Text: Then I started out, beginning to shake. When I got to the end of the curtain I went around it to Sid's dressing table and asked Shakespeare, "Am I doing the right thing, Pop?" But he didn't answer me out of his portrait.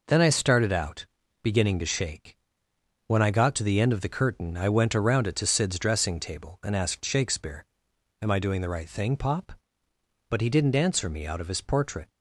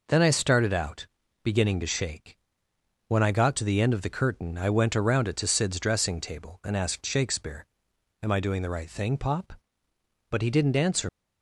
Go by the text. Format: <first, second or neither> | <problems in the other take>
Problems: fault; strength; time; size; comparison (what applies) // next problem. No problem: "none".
first | stops before "me out of his portrait"; at 11.0 s